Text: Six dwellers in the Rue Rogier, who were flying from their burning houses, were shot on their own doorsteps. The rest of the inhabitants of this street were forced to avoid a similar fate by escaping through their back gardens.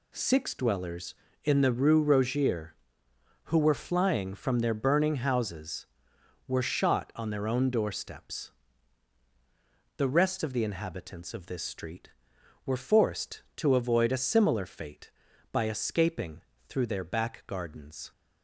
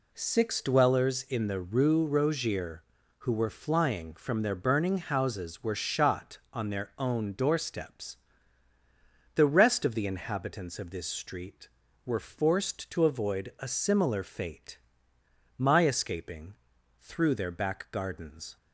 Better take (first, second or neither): first